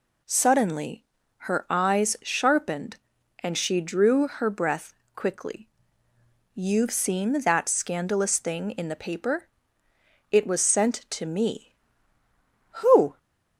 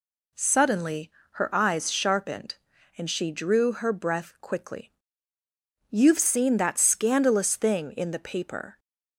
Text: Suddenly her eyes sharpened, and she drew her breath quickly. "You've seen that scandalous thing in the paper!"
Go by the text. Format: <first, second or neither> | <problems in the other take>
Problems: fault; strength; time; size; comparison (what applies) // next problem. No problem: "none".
second | pauses between "Suddenly" and "her"; slight; at 1.0 s; 0.34 s long; slight in the second // pauses between "breath" and "quickly"; slight; at 4.9 s; 0.22 s long // goes on to say "It was sent to me Who"; strong; from 10.3 s on; 2.8 s long